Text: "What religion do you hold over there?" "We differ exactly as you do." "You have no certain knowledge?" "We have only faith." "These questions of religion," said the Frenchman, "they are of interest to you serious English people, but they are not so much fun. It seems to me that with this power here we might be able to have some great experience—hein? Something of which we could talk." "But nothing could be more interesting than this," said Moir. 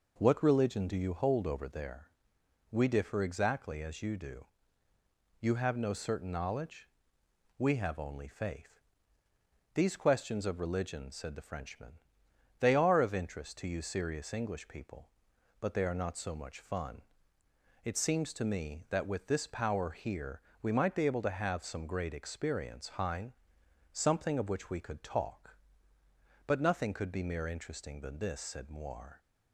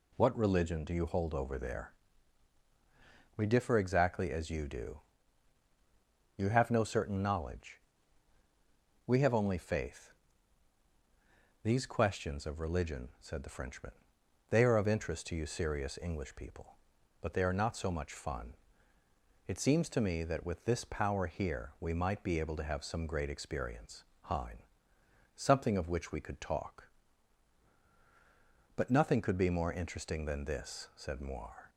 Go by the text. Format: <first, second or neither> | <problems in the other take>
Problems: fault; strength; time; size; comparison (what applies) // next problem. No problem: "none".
second | pauses between "here" and "we"; slight; at 20.4 s; 0.22 s long // says "mere" for "more"; at 27.2 s